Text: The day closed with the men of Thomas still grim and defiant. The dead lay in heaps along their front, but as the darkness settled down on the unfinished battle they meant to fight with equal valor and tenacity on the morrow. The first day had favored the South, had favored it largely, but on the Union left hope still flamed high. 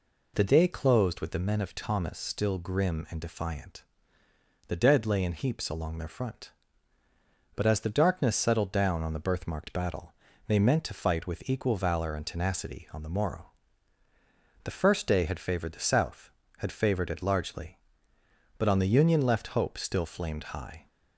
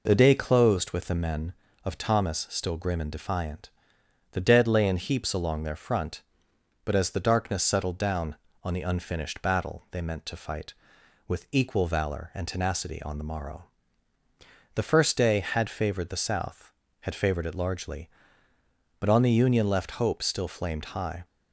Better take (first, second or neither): second